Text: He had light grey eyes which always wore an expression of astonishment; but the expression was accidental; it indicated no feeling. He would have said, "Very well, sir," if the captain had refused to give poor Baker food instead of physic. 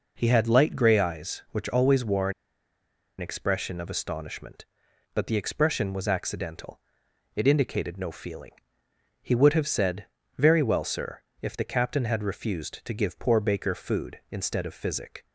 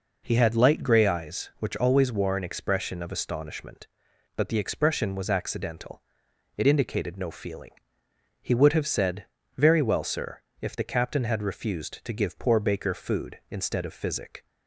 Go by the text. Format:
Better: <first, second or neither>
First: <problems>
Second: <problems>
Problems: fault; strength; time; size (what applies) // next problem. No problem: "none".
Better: second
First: pauses between "wore" and "an"; noticeable; at 2.3 s; 0.87 s long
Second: none